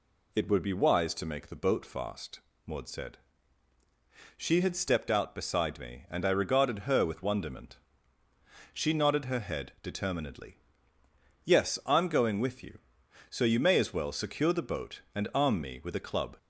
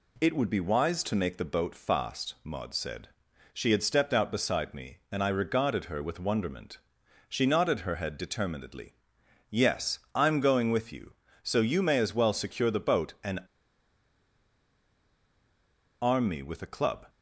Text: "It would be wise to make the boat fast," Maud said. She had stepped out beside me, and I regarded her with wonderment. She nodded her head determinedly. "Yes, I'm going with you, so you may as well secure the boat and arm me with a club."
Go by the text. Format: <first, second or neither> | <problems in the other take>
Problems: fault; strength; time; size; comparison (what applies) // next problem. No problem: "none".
first | pauses between "and" and "arm"; strong; at 13.4 s; 2.6 s long